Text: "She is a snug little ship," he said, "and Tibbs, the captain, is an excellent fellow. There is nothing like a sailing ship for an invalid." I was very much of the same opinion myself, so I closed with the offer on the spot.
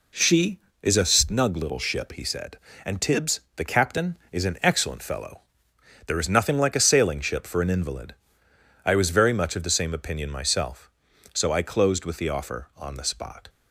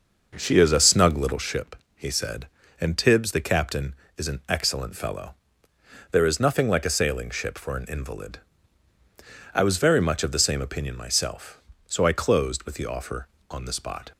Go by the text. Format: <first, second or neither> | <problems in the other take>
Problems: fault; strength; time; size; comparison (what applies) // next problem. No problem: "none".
first | starts louder than the rest; noticeable; until 1.5 s; 6 dB